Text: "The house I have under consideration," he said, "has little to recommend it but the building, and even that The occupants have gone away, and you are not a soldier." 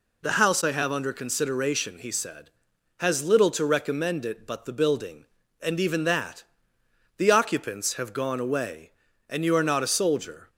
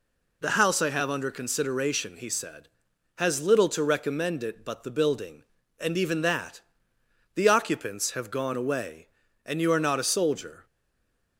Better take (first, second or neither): first